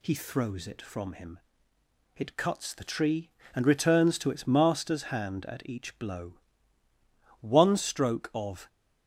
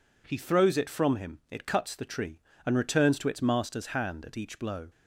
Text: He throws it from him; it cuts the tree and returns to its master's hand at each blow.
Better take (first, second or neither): second